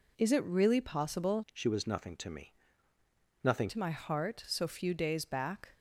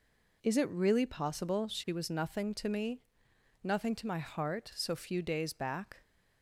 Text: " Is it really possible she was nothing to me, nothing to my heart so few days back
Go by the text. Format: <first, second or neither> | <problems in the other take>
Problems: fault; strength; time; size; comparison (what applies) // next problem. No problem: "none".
second | changes voice from "she" to "nothing"; from 1.5 to 3.7 s; 2.2 s long